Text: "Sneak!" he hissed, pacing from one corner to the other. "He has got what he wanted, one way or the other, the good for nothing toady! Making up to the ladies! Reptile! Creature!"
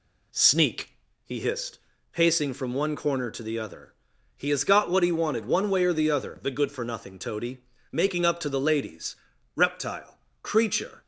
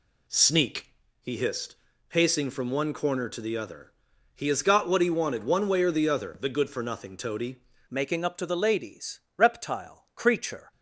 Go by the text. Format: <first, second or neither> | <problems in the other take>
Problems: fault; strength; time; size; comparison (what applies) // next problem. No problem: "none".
first | changes voice at "Making"; from 7.9 s on; 2.8 s long